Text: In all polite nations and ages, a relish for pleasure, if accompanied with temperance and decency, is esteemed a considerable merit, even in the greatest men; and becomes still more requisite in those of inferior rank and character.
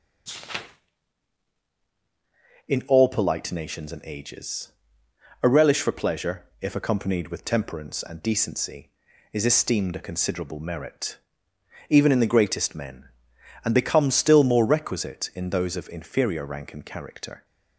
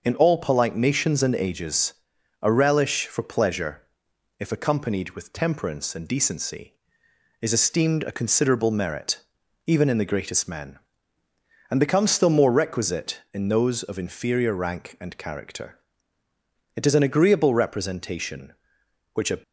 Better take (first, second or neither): first